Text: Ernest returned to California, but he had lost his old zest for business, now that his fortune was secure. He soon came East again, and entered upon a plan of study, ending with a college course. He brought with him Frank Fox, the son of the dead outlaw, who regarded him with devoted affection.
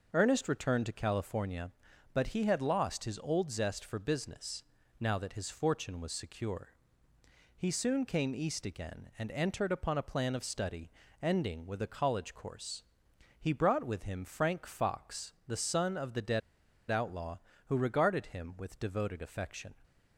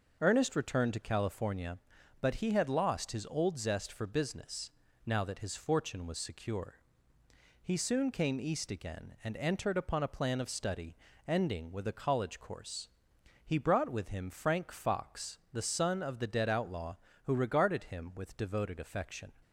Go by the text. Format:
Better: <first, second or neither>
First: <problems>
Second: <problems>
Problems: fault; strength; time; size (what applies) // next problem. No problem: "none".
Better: second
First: pauses between "dead" and "outlaw"; noticeable; at 16.4 s; 0.49 s long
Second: none